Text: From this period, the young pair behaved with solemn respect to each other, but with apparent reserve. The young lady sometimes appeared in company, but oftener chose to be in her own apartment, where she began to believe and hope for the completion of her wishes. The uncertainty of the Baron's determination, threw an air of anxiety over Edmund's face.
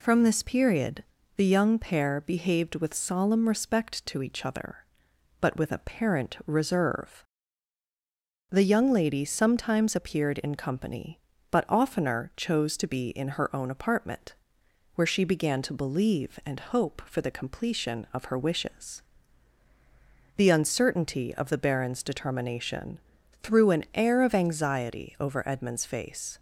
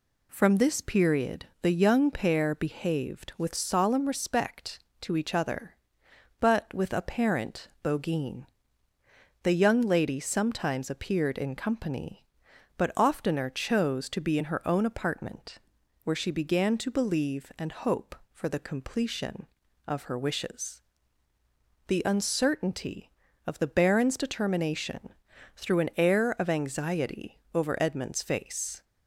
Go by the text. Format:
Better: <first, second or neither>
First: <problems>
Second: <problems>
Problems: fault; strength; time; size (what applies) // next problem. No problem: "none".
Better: first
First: none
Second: says "bogeen" for "reserve"; at 7.8 s